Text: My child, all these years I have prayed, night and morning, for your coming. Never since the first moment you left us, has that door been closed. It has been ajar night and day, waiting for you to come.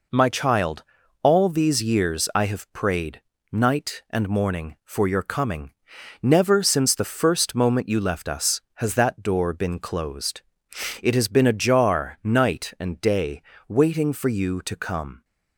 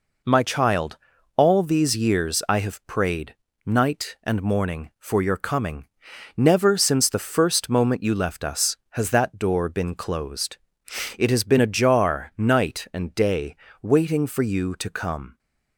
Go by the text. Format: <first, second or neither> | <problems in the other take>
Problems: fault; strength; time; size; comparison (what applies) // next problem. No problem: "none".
neither | none